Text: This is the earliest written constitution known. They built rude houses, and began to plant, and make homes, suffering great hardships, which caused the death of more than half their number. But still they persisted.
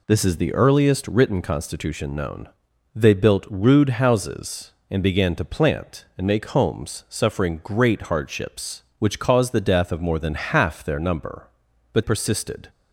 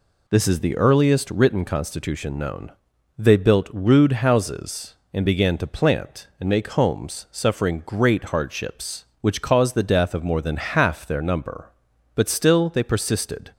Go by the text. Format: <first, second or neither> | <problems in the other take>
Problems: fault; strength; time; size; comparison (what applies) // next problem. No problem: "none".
second | skips "still they"; at 12.0 s